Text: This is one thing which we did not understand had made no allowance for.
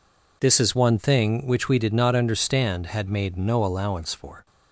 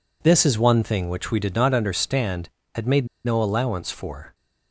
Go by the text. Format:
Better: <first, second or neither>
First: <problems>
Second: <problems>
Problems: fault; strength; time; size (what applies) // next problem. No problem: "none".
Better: first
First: none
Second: pauses between "made" and "no"; slight; at 3.0 s; 0.17 s long